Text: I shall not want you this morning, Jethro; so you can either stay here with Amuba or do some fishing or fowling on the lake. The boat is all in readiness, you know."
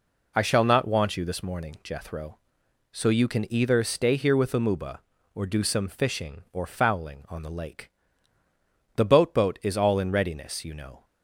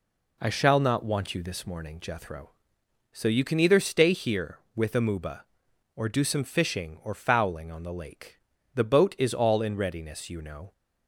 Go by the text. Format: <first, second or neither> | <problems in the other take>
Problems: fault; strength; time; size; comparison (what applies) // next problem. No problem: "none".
second | says "boat" twice; at 9.3 s